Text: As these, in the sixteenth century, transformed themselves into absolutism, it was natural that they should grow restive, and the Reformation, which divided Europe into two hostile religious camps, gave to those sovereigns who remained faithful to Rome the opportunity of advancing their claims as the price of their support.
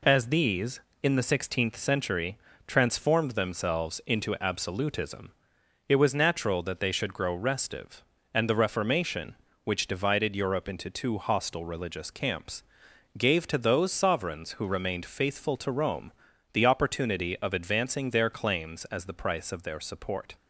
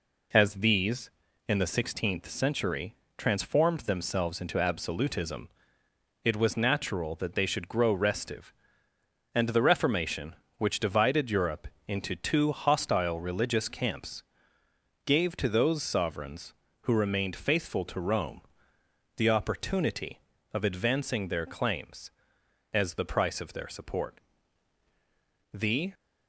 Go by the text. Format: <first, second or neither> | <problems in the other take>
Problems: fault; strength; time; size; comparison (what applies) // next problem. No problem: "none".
first | pauses between "Europe" and "into"; slight; at 11.6 s; 0.20 s long // pauses between "Rome" and "the"; noticeable; at 18.4 s; 0.76 s long; also in the first // goes on to say "The"; slight; from 25.5 s on; 0.40 s long